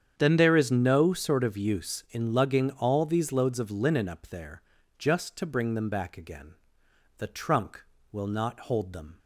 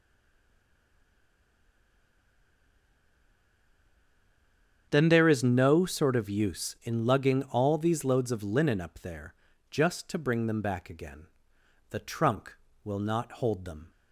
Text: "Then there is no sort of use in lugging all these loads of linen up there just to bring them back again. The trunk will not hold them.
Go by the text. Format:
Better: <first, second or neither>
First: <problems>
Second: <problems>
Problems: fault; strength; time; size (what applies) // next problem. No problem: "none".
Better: first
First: starts louder than the rest; strong; until 1.1 s; 8 dB // pauses between "there" and "just"; slight; at 4.6 s; 0.36 s long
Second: stays silent before the first word; strong; until 4.8 s; 4.8 s long // starts louder than the rest; strong; until 5.9 s; 8 dB // pauses between "there" and "just"; slight; at 9.3 s; 0.36 s long